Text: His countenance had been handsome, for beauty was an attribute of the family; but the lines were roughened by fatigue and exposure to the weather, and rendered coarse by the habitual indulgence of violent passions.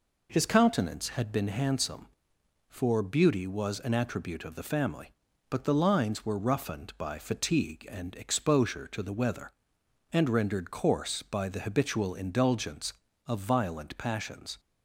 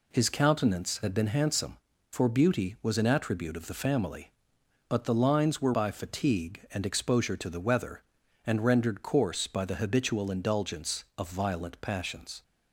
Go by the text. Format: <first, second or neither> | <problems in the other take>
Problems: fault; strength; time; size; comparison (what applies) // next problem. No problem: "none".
first | skips "roughened"; at 5.7 s